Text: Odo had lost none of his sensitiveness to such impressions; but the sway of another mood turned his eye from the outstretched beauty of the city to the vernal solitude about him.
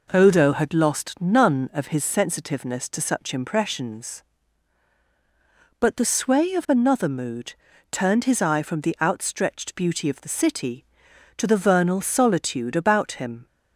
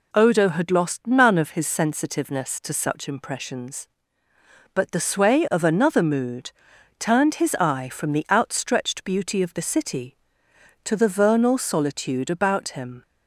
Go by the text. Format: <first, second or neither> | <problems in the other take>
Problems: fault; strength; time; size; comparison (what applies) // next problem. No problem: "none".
neither | pauses between "mood" and "turned"; the same in both